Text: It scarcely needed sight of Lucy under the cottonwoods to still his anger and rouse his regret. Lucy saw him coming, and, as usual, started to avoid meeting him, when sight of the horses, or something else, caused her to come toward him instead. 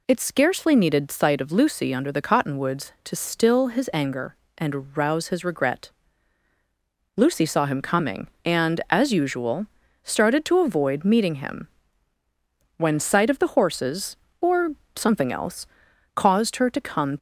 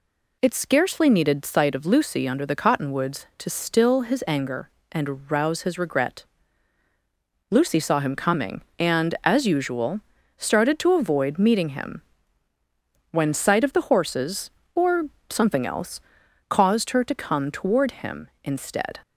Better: second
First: pauses between "or" and "something"; slight; at 14.7 s; 0.22 s long // stops before "toward him instead"; at 17.1 s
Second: pauses between "or" and "something"; slight; at 15.0 s; 0.22 s long

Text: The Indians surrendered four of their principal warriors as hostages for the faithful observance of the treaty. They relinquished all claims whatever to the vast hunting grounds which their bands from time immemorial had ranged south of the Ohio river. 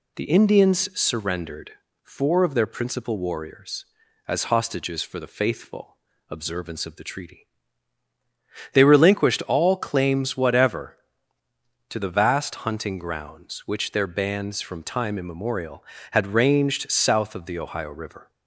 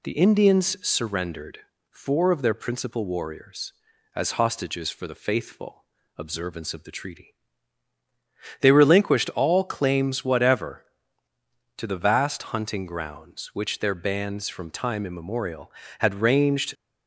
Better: first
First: pauses between "surrendered" and "four"; slight; at 1.7 s; 0.32 s long // pauses between "faithful" and "observance"; slight; at 5.9 s; 0.34 s long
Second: pauses between "surrendered" and "four"; slight; at 1.5 s; 0.32 s long // pauses between "faithful" and "observance"; slight; at 5.8 s; 0.34 s long // stops before "south of the Ohio river"; at 16.7 s

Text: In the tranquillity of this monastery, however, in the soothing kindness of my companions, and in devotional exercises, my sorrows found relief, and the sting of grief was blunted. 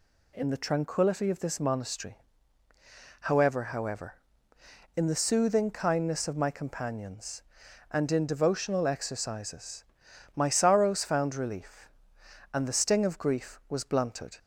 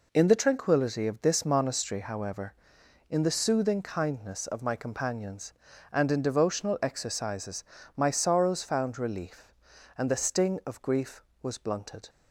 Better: second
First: says "however" twice; at 3.6 s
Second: none

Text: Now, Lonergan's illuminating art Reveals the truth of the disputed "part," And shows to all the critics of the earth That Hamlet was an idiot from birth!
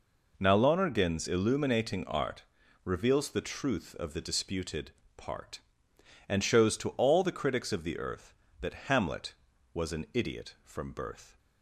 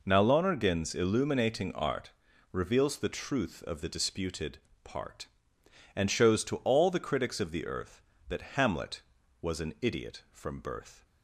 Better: neither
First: pauses between "art" and "Reveals"; at 2.4 s; 0.42 s long // pauses between "disputed" and "part"; slight; at 4.9 s; 0.24 s long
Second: pauses between "art" and "Reveals"; at 2.1 s; 0.42 s long // pauses between "disputed" and "part"; slight; at 4.5 s; 0.24 s long

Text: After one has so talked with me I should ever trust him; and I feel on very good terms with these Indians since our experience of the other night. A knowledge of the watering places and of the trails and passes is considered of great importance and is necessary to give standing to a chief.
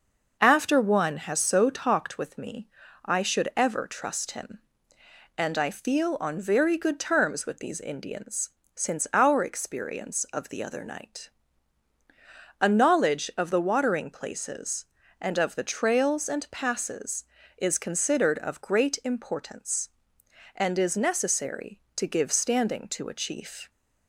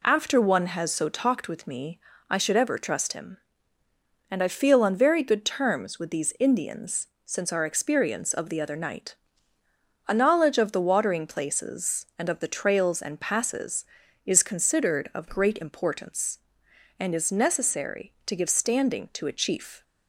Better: neither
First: pauses between "me" and "I"; slight; at 2.6 s; 0.36 s long // pauses between "Indians" and "since"; slight; at 8.4 s; 0.26 s long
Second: pauses between "me" and "I"; slight; at 1.9 s; 0.28 s long // pauses between "Indians" and "since"; slight; at 7.0 s; 0.18 s long

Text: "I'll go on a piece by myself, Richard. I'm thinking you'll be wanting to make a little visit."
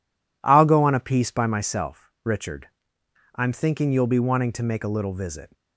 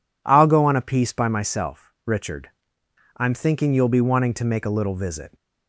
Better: second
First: gets quieter; strong; throughout; 7.5 dB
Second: none

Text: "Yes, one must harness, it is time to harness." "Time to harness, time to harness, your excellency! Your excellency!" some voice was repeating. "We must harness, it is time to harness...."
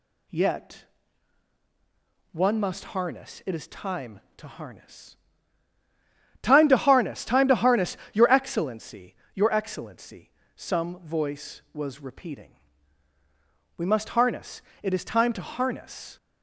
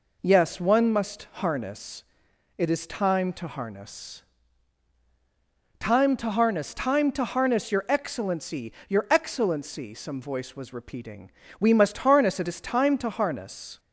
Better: second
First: says "Yet" for "Yes"; at 0.2 s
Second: none

